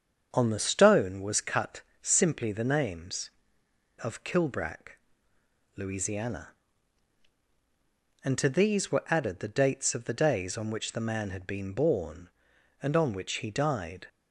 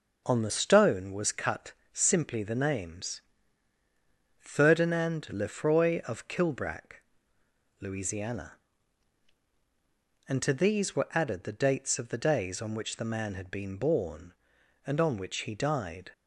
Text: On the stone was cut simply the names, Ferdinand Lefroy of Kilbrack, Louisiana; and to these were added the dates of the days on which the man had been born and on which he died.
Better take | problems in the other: second | starts louder than the rest; strong; until 1.3 s; 7 dB // pauses between "cut" and "simply"; slight; at 1.8 s; 0.22 s long; slight in the second // skips "Ferdinand Lefroy"; at 3.6 s

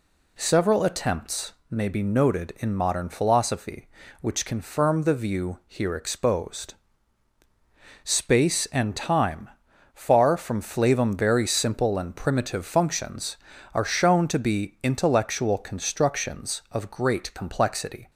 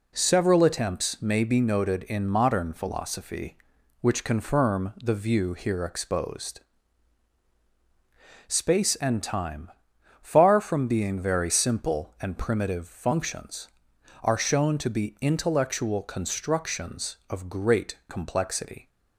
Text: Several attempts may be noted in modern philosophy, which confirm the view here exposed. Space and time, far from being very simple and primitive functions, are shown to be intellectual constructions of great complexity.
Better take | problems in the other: second | pauses between "attempts" and "may"; slight; at 1.5 s; 0.18 s long // says "flavum" for "being"; at 10.6 s

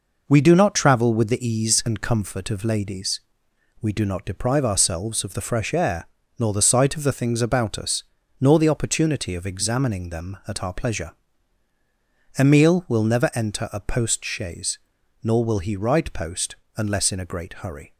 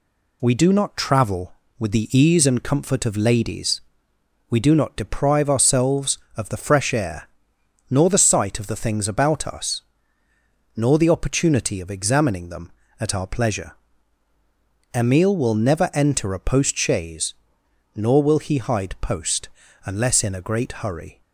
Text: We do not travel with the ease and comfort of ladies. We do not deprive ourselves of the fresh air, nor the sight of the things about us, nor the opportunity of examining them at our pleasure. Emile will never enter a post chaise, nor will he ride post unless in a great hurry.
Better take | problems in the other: first | says "hide" for "ride"; at 18.5 s // pauses between "post" and "unless"; slight; at 19.4 s; 0.36 s long; slight in the first

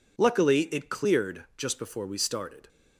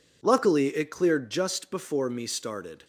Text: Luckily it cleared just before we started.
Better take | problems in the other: first | says "me" for "we"; at 2.0 s

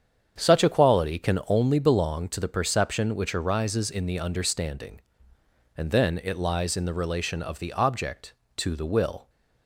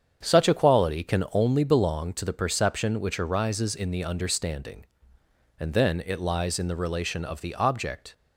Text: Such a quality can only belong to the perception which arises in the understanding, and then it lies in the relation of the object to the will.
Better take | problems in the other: first | starts louder than the rest; strong; until 1.2 s; 7.5 dB; strong in the first // stops before "to the will"; at 8.1 s

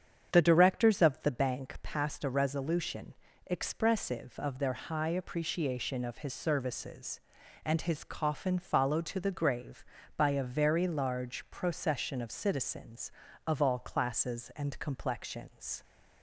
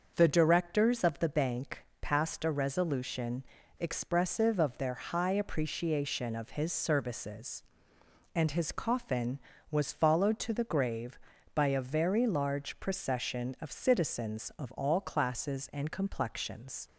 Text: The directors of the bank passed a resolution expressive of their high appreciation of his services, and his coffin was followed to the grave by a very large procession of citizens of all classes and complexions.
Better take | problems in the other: second | starts louder than the rest; strong; until 1.3 s; 8 dB; also in the second // pauses between "resolution" and "expressive"; slight; at 3.1 s; 0.32 s long; also in the second // skips "was"; at 8.5 s

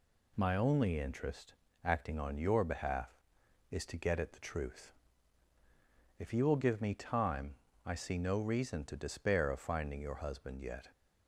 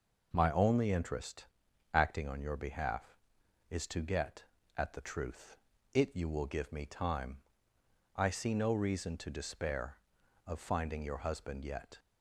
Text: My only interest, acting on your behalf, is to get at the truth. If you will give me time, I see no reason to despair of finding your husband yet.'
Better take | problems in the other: first | says "It" for "If"; at 5.9 s

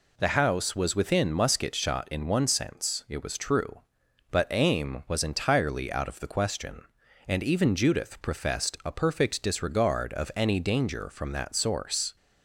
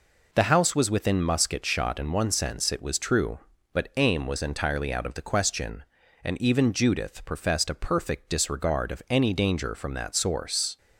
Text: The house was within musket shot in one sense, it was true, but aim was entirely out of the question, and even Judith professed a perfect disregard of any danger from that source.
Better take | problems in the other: neither | none

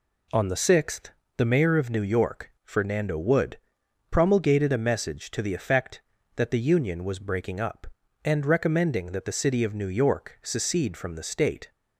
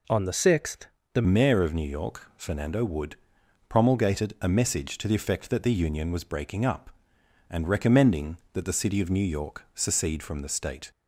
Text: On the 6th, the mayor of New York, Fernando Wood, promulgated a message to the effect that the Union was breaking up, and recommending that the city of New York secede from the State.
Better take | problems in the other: first | changes voice at "mayor"; from 1.2 s on; 9.6 s long

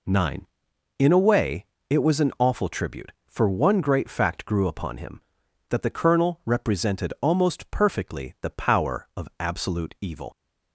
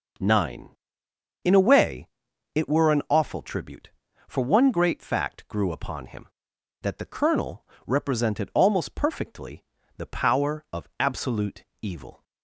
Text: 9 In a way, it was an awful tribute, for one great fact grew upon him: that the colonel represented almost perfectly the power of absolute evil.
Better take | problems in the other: first | says "were" for "was"; at 2.6 s // pauses between "colonel" and "represented"; slight; at 7.6 s; 0.22 s long // pauses between "perfectly" and "the"; slight; at 9.6 s; 0.34 s long // pauses between "absolute" and "evil"; slight; at 11.6 s; 0.18 s long

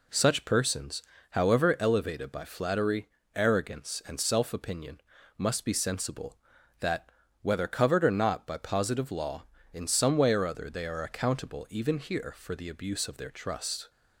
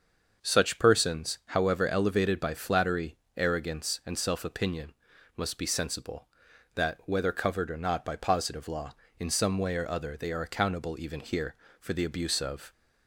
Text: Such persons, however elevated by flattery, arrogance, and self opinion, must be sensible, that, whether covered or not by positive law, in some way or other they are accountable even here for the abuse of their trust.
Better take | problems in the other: first | starts louder than the rest; until 1.5 s; 6.5 dB // stops before "their trust"; at 12.7 s

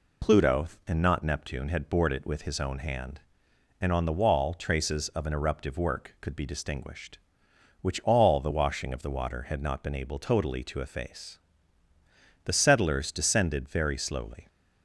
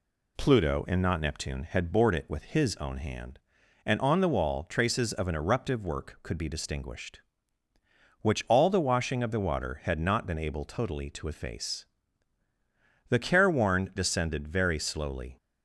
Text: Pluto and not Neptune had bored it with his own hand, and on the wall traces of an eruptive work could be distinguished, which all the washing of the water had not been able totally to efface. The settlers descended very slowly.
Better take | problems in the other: first | says "careworn" for "settlers"; at 13.1 s

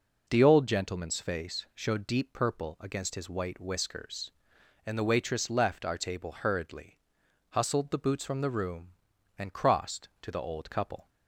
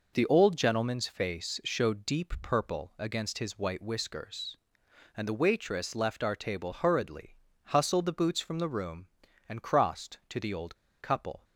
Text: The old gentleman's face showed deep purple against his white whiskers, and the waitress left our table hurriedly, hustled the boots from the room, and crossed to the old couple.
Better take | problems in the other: first | pauses between "old" and "couple"; slight; at 10.7 s; 0.25 s long

